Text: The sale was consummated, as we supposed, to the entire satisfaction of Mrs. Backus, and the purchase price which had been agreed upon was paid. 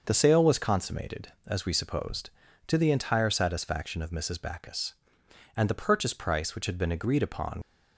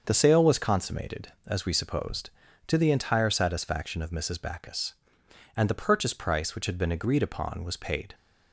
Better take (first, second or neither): second